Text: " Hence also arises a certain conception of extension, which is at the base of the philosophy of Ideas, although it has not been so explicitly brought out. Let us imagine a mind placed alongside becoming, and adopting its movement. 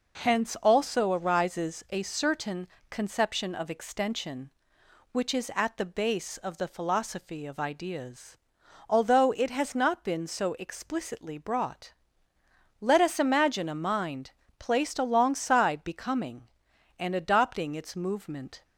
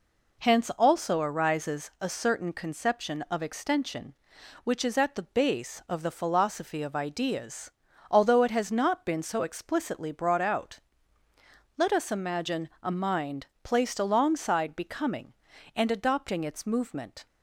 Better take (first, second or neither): second